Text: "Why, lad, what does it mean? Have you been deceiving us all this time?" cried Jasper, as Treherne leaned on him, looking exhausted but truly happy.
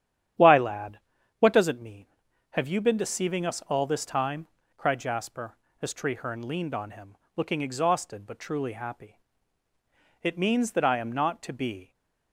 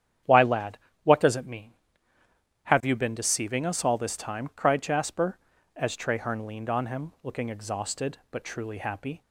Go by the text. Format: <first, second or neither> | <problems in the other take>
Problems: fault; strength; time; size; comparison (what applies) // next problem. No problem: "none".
second | starts louder than the rest; strong; until 1.7 s; 10 dB; strong in the second // goes on to say "It means that I am not to be"; strong; from 10.2 s on; 1.7 s long